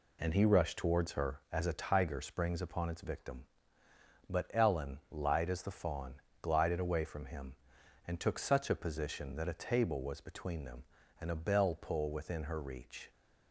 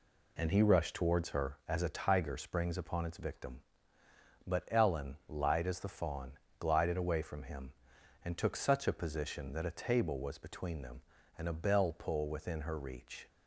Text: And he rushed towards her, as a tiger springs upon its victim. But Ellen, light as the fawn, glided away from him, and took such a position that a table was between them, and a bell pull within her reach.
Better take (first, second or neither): neither